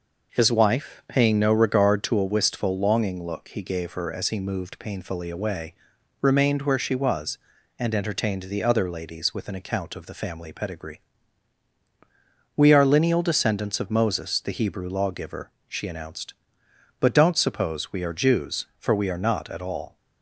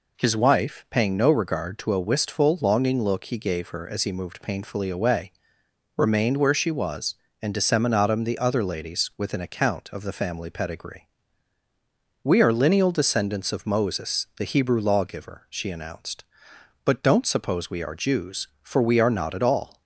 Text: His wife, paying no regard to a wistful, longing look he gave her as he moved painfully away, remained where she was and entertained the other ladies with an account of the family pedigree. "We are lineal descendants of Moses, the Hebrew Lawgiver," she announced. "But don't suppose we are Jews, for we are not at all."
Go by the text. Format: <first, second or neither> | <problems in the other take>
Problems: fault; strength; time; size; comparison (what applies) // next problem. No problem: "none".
first | says "disseminatum" for "entertained"; at 7.5 s